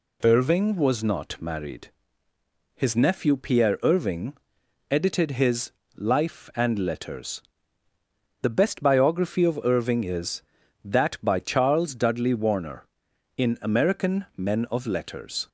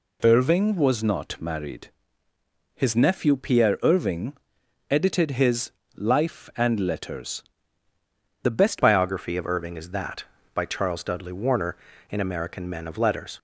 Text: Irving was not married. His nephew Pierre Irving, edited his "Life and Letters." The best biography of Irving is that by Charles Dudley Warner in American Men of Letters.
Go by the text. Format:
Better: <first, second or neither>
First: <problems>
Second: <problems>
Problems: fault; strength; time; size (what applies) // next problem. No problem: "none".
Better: first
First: pauses between "his" and "Life"; slight; at 5.7 s; 0.24 s long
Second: pauses between "his" and "Life"; slight; at 5.7 s; 0.24 s long // changes voice at "biography"; from 8.7 s on; 4.6 s long